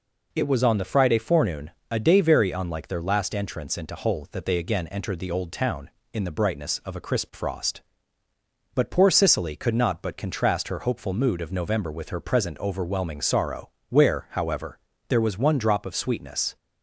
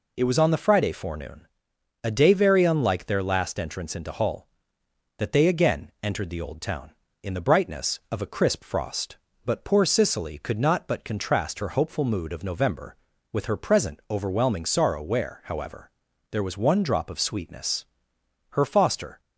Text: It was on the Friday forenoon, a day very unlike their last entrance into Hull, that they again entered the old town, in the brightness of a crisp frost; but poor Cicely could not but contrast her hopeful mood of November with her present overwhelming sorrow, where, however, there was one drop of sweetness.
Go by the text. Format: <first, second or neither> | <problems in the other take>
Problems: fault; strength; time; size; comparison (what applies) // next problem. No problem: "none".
first | goes on to say "Her foster"; noticeable; from 18.4 s on; 0.70 s long